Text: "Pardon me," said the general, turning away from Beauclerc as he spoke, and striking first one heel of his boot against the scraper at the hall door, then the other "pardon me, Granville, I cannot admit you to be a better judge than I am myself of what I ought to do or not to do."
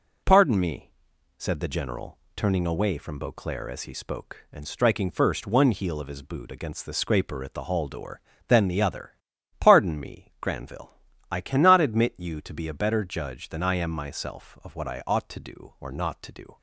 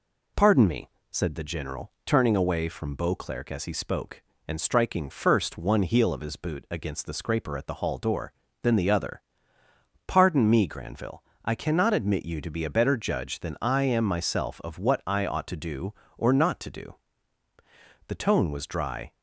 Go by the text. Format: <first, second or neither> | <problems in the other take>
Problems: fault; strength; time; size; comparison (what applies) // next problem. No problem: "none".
first | pauses between "other" and "pardon"; noticeable; at 9.2 s; 0.86 s long; also in the first // goes on to say "The tone was dry"; noticeable; from 18.0 s on; 1.0 s long